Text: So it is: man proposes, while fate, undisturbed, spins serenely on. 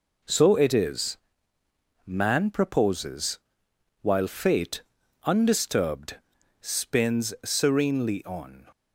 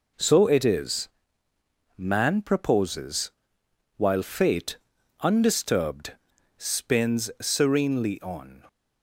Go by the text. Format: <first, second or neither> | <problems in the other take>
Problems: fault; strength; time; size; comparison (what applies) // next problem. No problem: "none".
neither | none